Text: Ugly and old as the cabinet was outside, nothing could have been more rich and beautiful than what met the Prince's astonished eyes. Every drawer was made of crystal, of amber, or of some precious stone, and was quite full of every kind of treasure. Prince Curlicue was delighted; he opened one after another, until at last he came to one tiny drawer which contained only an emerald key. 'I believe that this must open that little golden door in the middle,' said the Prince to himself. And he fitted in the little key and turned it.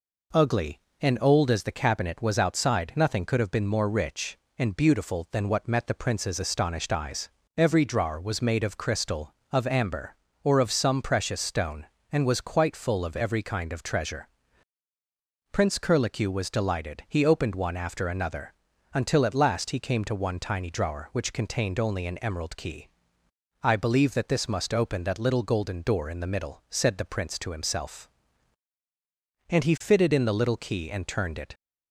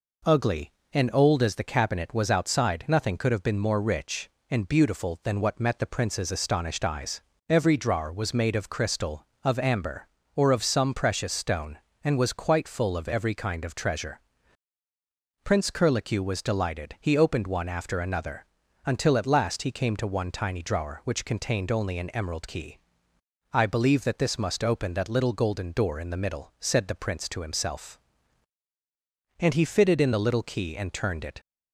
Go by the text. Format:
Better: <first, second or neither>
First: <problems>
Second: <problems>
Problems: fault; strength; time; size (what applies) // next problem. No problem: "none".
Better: neither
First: none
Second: none